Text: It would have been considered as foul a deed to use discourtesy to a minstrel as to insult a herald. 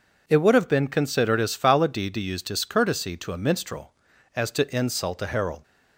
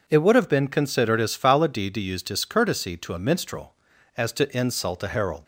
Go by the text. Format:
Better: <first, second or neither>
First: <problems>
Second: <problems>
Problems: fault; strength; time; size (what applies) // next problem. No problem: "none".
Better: neither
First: none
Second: none